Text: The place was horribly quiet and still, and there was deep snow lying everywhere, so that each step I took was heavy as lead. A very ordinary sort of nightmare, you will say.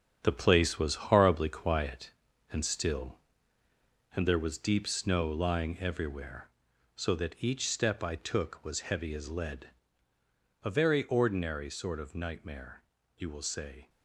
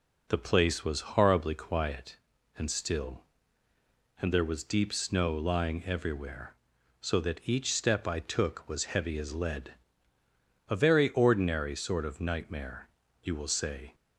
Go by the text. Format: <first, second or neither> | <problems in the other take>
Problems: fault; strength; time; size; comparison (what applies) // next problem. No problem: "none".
second | gets quieter; strong; throughout; 8.5 dB